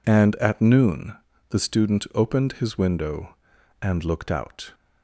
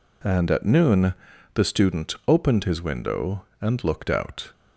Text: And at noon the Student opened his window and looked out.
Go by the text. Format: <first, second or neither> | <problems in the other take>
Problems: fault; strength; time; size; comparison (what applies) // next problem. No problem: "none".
neither | pauses between "noon" and "the"; the same in both